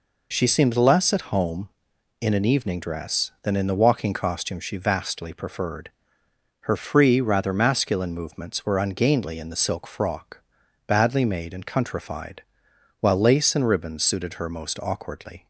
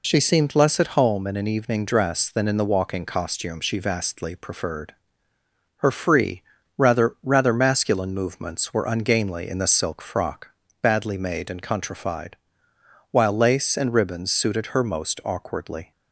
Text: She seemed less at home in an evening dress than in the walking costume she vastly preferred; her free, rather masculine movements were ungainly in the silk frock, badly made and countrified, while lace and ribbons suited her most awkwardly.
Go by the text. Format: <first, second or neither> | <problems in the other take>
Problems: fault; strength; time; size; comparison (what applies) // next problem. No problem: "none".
first | says "rather" twice; at 7.2 s